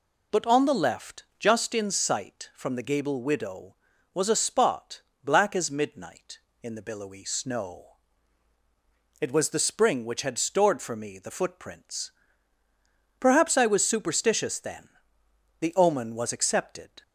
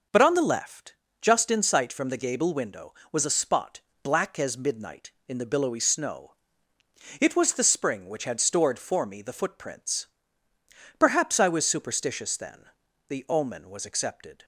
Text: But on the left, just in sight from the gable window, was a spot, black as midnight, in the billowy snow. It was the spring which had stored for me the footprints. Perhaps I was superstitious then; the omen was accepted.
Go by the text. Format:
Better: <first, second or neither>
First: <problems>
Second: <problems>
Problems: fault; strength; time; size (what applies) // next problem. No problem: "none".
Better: second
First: says "widow" for "window"; at 3.2 s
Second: none